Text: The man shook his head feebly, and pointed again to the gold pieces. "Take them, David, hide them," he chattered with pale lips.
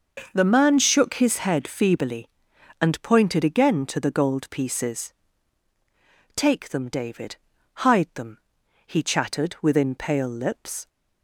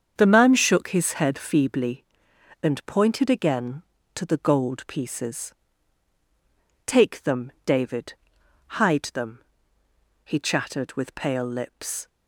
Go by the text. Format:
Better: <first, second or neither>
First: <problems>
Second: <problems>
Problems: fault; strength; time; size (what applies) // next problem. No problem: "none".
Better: second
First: starts louder than the rest; noticeable; until 1.3 s; 6 dB // says "within" for "with"; at 9.6 s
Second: starts louder than the rest; strong; until 1.1 s; 7.5 dB